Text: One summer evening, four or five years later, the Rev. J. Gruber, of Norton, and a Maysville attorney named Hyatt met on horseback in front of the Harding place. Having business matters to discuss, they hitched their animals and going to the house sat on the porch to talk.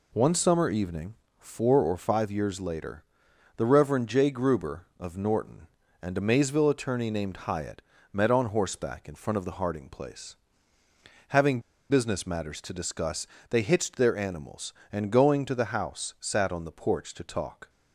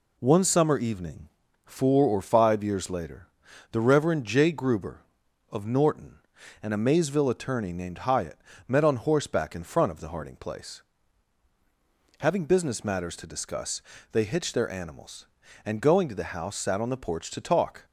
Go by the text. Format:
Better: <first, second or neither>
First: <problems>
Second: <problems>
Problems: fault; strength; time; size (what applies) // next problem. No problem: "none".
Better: second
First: pauses between "Hyatt" and "met"; slight; at 7.8 s; 0.32 s long // pauses between "Having" and "business"; slight; at 11.6 s; 0.29 s long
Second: pauses between "Hyatt" and "met"; slight; at 8.3 s; 0.30 s long